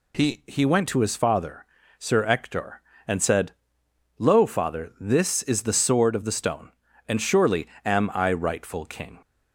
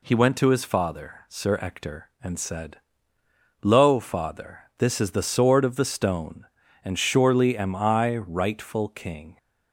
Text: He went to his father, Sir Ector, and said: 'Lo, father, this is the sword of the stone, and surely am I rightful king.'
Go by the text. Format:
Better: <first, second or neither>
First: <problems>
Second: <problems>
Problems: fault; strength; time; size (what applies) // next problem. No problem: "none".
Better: second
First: says "He" twice; at 0.4 s // pauses between "surely" and "am"; slight; at 7.6 s; 0.16 s long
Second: none